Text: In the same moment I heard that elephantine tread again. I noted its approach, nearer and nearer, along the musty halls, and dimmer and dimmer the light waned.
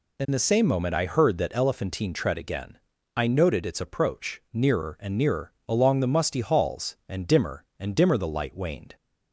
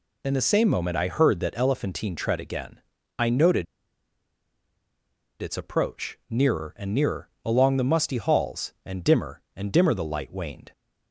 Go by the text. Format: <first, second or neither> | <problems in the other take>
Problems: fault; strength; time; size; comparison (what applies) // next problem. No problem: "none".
first | pauses between "noted" and "its"; strong; at 3.6 s; 1.7 s long